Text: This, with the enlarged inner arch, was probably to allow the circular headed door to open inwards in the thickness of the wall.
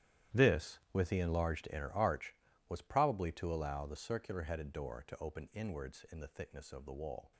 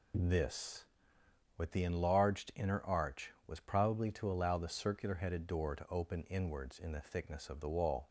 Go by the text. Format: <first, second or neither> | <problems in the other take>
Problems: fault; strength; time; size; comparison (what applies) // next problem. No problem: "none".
second | gets quieter; strong; throughout; 16 dB